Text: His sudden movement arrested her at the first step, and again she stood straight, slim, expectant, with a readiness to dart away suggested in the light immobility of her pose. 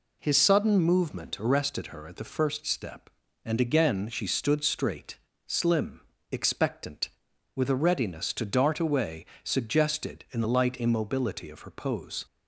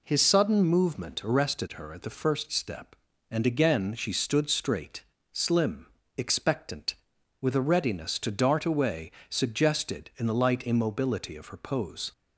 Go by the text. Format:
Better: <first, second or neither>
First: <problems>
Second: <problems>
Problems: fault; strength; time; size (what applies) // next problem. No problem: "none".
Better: neither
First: pauses between "away" and "suggested"; slight; at 9.2 s; 0.20 s long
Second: pauses between "away" and "suggested"; slight; at 9.0 s; 0.20 s long